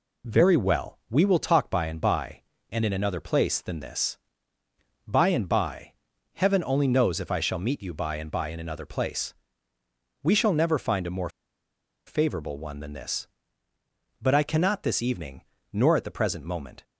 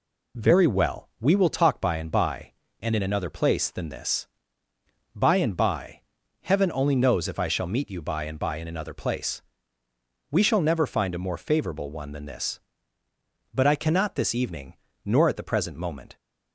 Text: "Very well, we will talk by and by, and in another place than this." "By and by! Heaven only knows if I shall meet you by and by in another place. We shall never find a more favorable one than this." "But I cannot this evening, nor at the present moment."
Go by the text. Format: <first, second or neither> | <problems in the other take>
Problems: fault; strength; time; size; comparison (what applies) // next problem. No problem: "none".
second | pauses between "more" and "favorable"; noticeable; at 11.2 s; 0.76 s long